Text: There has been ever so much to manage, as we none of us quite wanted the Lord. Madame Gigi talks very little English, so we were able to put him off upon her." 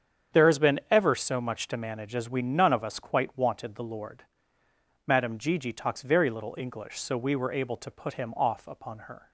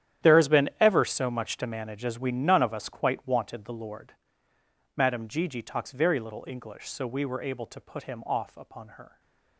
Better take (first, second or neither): first